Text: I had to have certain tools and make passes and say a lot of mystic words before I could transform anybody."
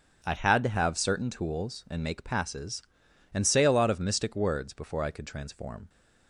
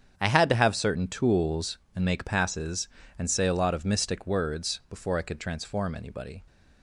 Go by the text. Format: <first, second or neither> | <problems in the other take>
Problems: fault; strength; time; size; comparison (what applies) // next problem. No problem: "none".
second | starts louder than the rest; strong; until 1.2 s; 7 dB; strong in the second // stops before "anybody"; at 5.8 s